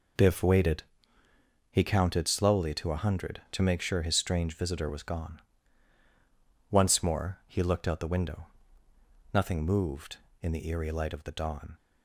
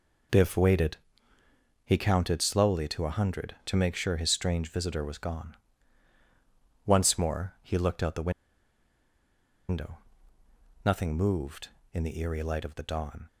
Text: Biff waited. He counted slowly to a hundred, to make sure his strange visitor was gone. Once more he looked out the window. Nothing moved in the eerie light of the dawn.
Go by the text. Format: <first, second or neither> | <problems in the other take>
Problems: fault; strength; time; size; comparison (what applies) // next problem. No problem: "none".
first | pauses between "the" and "window"; strong; at 8.3 s; 1.3 s long